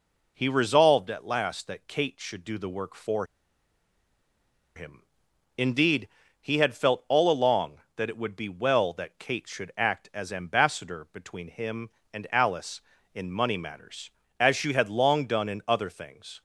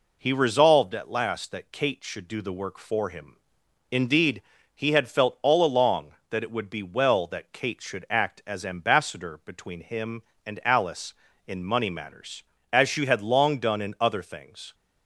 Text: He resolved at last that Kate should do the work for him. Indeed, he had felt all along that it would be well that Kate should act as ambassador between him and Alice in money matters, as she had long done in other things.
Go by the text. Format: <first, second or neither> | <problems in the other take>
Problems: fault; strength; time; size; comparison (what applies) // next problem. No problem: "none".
second | pauses between "for" and "him"; strong; at 3.2 s; 1.5 s long